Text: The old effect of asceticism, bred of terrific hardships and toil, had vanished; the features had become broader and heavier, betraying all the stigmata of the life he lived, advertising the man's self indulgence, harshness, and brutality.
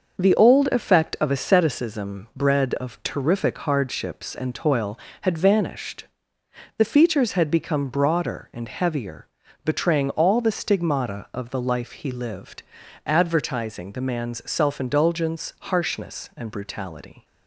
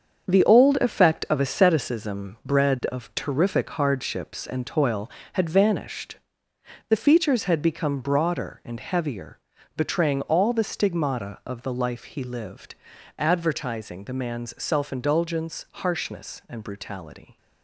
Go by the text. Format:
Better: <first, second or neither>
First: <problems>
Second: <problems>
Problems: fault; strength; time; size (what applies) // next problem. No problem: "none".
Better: first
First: starts louder than the rest; until 1.2 s; 6 dB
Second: gets quieter; strong; throughout; 8.5 dB // starts louder than the rest; until 1.3 s; 7 dB